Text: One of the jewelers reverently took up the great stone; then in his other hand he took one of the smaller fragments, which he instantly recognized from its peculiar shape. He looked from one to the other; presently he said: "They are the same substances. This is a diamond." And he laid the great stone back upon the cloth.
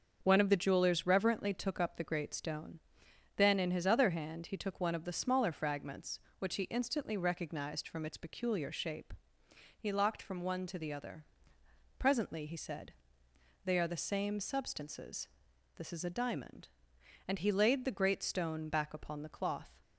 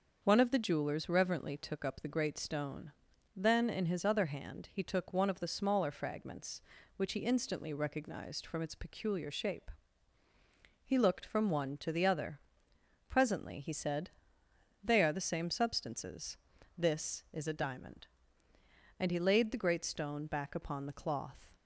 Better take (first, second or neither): second